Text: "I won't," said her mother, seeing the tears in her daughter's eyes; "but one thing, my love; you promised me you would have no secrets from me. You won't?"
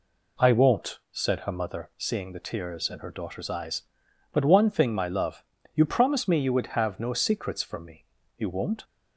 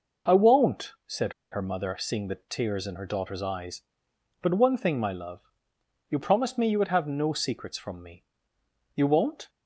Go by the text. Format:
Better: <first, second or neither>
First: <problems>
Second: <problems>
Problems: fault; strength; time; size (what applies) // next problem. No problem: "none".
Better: first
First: none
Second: pauses between "said" and "her"; slight; at 1.3 s; 0.20 s long